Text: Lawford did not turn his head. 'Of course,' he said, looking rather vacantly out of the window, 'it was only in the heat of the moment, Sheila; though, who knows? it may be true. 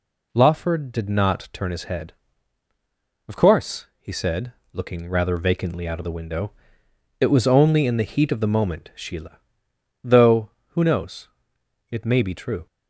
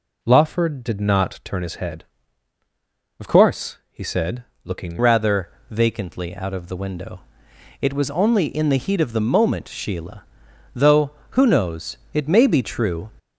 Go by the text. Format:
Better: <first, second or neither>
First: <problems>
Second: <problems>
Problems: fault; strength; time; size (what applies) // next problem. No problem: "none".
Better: first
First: none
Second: changes voice at "rather"; from 4.9 s on; 8.1 s long // pauses between "rather" and "vacantly"; slight; at 5.4 s; 0.22 s long